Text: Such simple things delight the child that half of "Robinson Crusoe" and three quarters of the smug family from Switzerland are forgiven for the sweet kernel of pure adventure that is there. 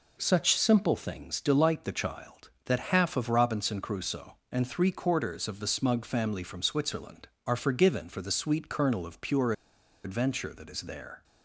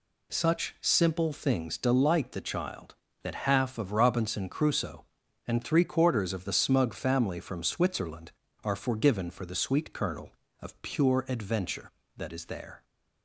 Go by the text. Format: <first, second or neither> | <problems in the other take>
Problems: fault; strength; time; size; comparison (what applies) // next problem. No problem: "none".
second | pauses between "pure" and "adventure"; noticeable; at 9.5 s; 0.52 s long